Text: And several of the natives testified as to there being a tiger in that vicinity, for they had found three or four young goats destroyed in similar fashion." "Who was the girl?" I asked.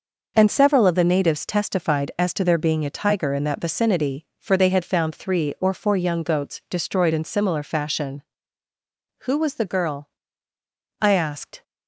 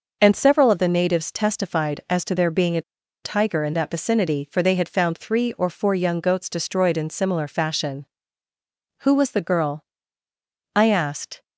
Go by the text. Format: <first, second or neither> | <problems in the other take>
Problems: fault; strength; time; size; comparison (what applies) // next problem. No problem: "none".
first | pauses between "a" and "tiger"; at 2.8 s; 0.42 s long